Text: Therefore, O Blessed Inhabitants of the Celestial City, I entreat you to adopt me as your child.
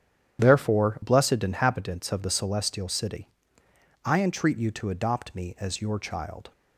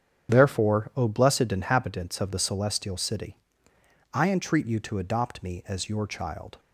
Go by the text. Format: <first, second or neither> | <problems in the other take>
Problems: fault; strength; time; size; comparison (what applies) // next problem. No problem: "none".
second | starts louder than the rest; strong; until 1.4 s; 9.5 dB; strong in the second // skips "O"; at 1.0 s